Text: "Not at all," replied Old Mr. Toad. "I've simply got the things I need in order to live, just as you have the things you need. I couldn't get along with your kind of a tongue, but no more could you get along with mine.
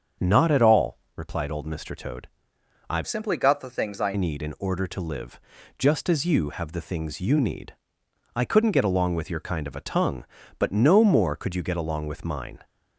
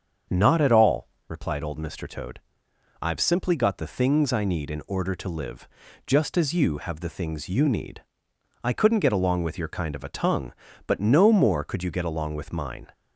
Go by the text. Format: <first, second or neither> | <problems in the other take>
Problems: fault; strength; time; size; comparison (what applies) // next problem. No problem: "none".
second | starts louder than the rest; until 1.3 s; 7 dB; strong in the second // changes voice from "simply" to "I"; from 3.0 to 4.1 s; 1.1 s long